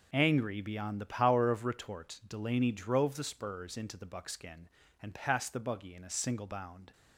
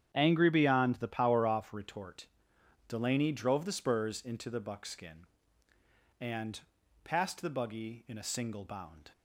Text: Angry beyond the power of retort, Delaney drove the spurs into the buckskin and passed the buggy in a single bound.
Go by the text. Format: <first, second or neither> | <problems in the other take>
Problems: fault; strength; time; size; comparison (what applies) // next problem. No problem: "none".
first | starts louder than the rest; strong; until 1.1 s; 9 dB // says "off" for "of"; at 1.4 s // pauses between "and" and "passed"; at 6.5 s; 0.42 s long